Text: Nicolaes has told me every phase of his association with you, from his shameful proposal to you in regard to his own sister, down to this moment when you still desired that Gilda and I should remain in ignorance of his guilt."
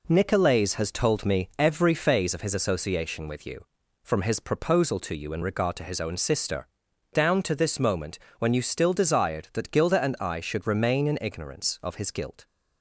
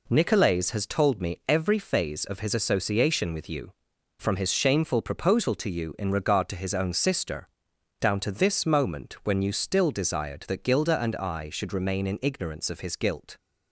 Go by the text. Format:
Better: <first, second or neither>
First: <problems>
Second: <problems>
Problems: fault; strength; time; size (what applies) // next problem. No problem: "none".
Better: second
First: skips "shameful"; at 4.3 s // pauses between "moment" and "when"; slight; at 8.1 s; 0.18 s long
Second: none